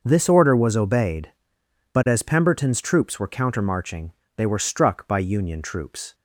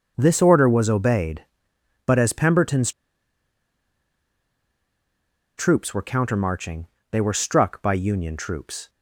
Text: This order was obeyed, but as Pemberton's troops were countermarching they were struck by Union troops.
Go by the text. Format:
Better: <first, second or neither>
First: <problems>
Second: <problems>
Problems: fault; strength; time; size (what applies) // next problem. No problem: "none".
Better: first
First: pauses between "countermarching" and "they"; slight; at 4.1 s; 0.26 s long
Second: starts louder than the rest; noticeable; until 1.1 s; 6 dB // pauses between "Pemberton's" and "troops"; strong; at 2.9 s; 2.6 s long // pauses between "countermarching" and "they"; slight; at 6.8 s; 0.26 s long